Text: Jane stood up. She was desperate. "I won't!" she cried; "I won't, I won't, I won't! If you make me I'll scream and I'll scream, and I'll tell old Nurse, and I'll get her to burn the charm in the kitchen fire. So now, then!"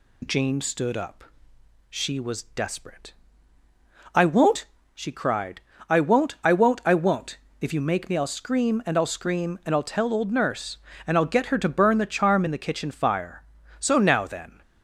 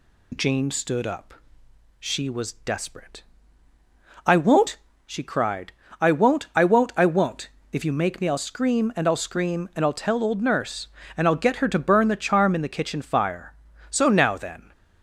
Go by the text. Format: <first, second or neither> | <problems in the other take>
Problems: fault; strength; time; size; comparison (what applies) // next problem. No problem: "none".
neither | none